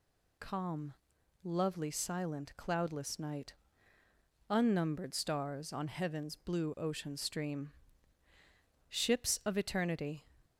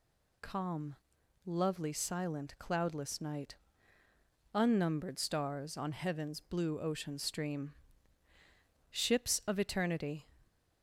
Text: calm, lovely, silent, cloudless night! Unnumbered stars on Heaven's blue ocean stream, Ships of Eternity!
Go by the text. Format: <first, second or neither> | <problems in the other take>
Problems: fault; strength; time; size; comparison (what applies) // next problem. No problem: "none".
neither | none